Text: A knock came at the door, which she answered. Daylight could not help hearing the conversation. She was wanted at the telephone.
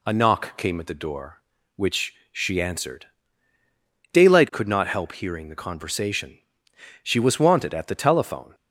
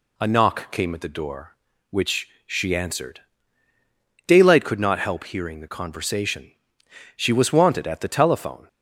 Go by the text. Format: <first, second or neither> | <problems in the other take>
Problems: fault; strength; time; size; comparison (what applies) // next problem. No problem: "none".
neither | pauses between "which" and "she"; slight; the same in both